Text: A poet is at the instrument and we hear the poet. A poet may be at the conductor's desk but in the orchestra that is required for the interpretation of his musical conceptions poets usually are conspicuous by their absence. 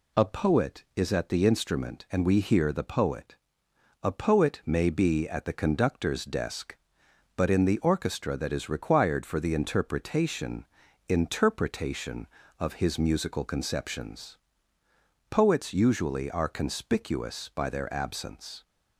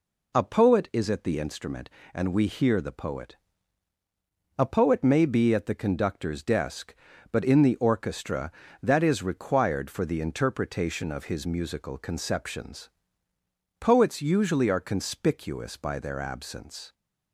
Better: second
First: says "interpretation" twice; at 11.0 s // pauses between "conceptions" and "poets"; noticeable; at 14.3 s; 0.94 s long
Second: pauses between "conceptions" and "poets"; noticeable; at 12.8 s; 0.92 s long

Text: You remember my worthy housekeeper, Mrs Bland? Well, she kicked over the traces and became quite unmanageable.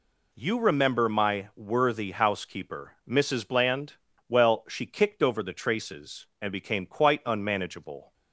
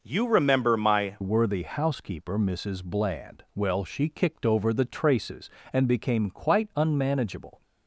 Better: first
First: none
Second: changes voice at "worthy"; from 1.2 s on; 6.4 s long

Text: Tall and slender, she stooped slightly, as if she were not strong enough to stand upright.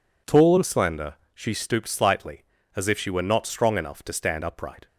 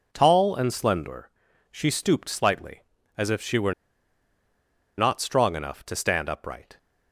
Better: first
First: none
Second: pauses between "were" and "not"; at 3.7 s; 1.2 s long

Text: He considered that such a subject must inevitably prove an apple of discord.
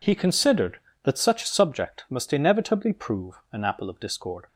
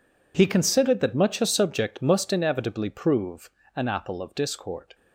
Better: first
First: pauses between "prove" and "an"; slight; at 3.3 s; 0.18 s long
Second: says "much" for "such"; at 1.1 s // pauses between "prove" and "an"; slight; at 3.5 s; 0.26 s long

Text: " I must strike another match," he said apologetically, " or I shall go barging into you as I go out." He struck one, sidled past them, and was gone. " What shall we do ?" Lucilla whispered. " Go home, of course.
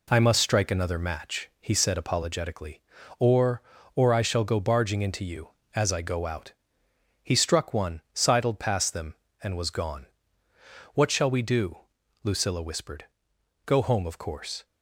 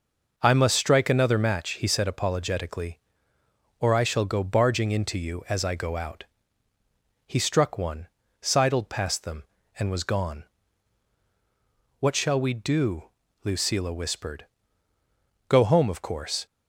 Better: second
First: says "or" twice; at 3.9 s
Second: none

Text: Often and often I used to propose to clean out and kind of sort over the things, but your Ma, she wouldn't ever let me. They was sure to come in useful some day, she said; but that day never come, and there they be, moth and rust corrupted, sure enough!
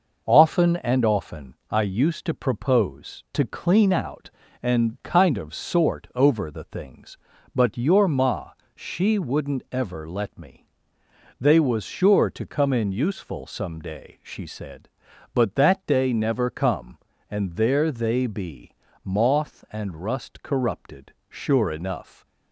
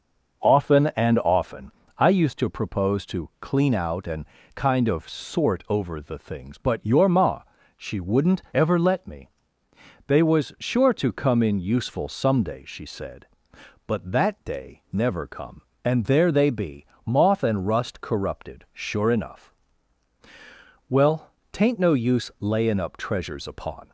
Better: first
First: none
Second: pauses between "often" and "I"; slight; at 1.6 s; 0.28 s long // pauses between "and" and "kind"; slight; at 4.2 s; 0.30 s long // goes on to say "Well tain't no use layin up treasures upon"; strong; from 20.8 s on; 3.0 s long

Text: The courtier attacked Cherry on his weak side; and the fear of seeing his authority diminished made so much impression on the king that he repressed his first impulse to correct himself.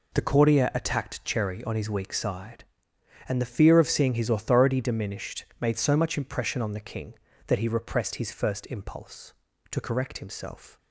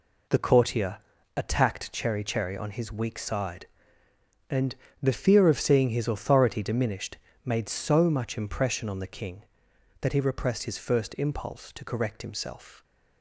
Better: first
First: none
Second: pauses between "courtier" and "attacked"; at 0.9 s; 0.40 s long // says "Cherry" twice; at 2.2 s // pauses between "and" and "the"; slight; at 4.7 s; 0.24 s long // pauses between "diminished" and "made"; slight; at 7.1 s; 0.28 s long

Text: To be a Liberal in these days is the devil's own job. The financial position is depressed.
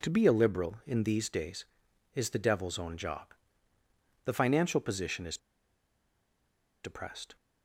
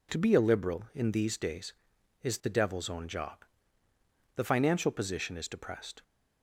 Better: second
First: pauses between "is" and "depressed"; strong; at 5.3 s; 1.4 s long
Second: none

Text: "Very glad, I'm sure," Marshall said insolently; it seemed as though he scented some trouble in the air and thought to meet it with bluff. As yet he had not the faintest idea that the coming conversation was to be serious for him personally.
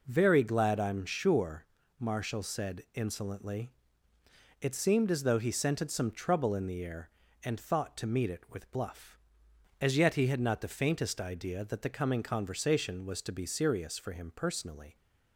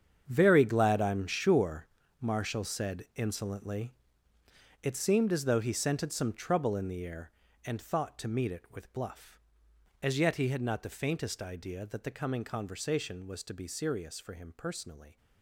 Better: first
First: none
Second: gets quieter; strong; throughout; 12.5 dB

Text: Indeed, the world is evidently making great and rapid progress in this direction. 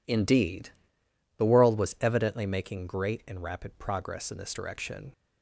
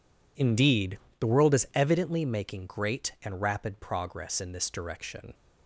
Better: second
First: says "was" for "is"; at 1.7 s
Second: none

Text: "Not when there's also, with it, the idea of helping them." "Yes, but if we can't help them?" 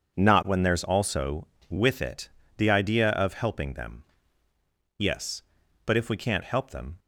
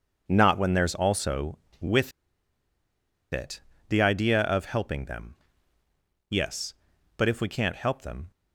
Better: first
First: none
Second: pauses between "with" and "it"; at 2.1 s; 1.2 s long

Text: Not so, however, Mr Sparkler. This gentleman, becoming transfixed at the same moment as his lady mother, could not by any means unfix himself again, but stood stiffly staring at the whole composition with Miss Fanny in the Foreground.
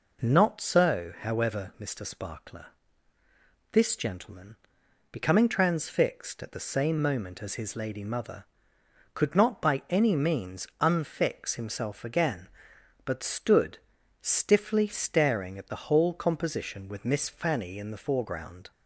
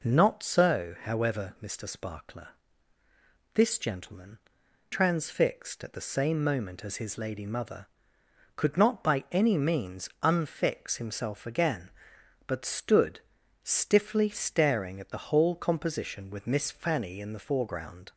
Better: first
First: pauses between "stood" and "stiffly"; at 13.7 s; 0.42 s long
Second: skips "becoming"; at 4.6 s // pauses between "stood" and "stiffly"; at 13.2 s; 0.42 s long

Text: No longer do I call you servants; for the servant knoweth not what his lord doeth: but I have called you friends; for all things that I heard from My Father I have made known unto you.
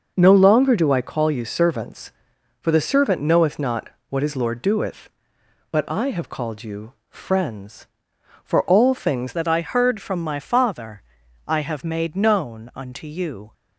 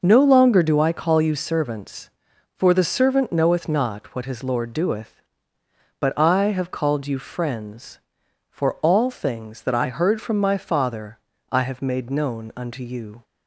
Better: second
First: pauses between "not" and "what"; slight; at 3.8 s; 0.22 s long // pauses between "you" and "friends"; slight; at 6.9 s; 0.16 s long // changes voice at "that"; from 9.3 s on; 4.2 s long // pauses between "Father" and "I"; at 11.0 s; 0.44 s long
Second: pauses between "Father" and "I"; slight; at 11.1 s; 0.34 s long

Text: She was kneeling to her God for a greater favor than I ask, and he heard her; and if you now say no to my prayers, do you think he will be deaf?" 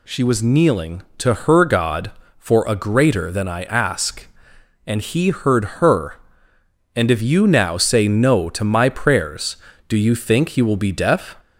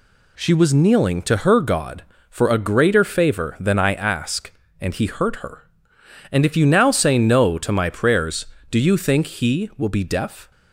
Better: second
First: skips "favor"; at 3.2 s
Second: none

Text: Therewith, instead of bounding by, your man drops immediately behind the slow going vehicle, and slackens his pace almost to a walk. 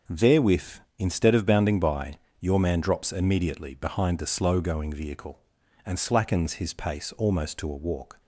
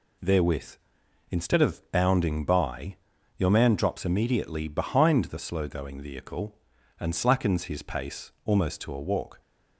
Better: neither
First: none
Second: none

